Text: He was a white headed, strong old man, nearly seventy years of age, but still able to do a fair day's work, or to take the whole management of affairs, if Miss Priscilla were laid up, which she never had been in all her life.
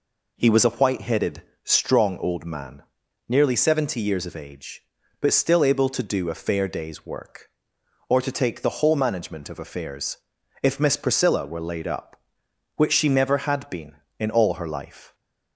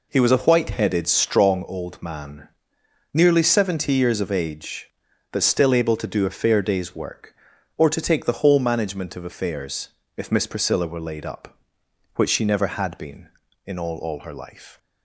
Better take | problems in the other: first | says "all" twice; at 13.9 s

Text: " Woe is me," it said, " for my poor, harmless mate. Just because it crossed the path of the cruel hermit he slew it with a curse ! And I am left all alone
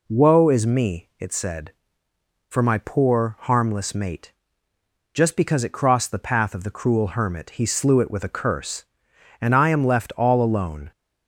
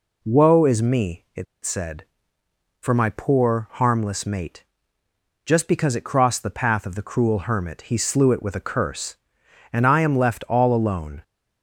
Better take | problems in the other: first | pauses between "it" and "said"; slight; at 1.4 s; 0.19 s long

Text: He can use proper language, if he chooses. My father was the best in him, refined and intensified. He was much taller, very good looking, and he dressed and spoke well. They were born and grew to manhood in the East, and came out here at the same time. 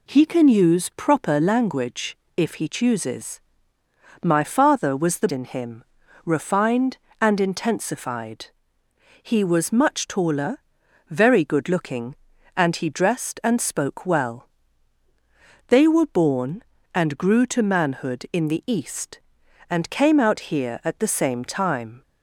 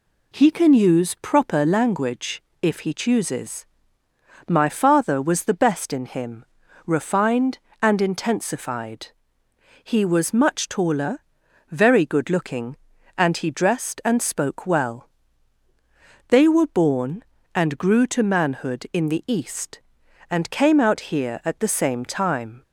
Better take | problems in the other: second | skips "best"; at 5.2 s

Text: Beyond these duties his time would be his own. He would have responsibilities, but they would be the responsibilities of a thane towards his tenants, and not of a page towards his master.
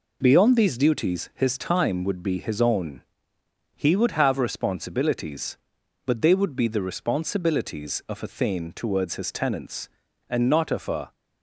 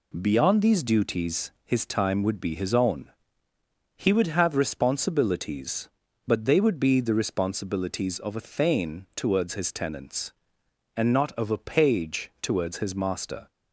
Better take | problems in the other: second | stops before "page towards his master"; at 11.1 s

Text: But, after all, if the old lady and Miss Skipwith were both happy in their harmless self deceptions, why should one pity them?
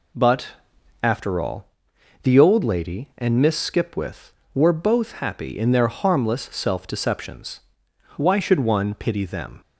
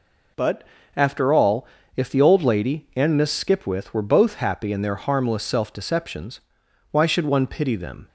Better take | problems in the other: second | skips "if"; at 1.9 s

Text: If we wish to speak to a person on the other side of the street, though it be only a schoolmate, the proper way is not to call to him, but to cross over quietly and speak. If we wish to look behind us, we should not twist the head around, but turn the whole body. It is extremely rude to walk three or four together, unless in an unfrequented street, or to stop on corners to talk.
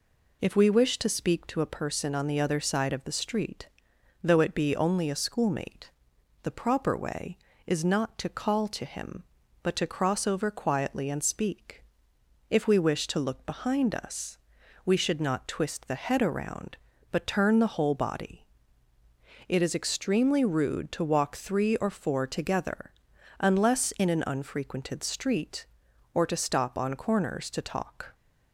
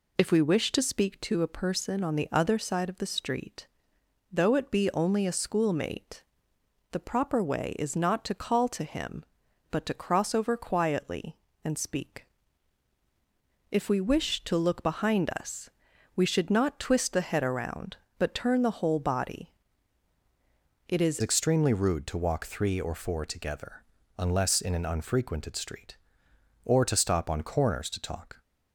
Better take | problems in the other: first | changes voice at "extremely"; from 21.2 s on; 7.2 s long

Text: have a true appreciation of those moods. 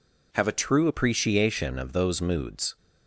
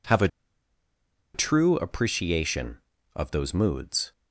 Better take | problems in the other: first | pauses between "a" and "true"; at 0.2 s; 1.0 s long

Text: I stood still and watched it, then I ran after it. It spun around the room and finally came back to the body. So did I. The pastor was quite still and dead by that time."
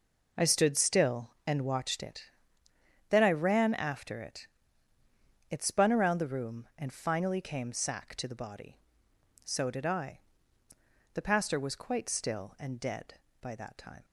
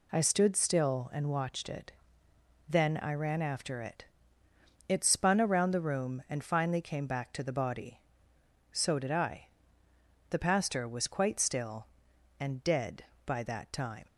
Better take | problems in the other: second | says "sack" for "back"; at 7.7 s

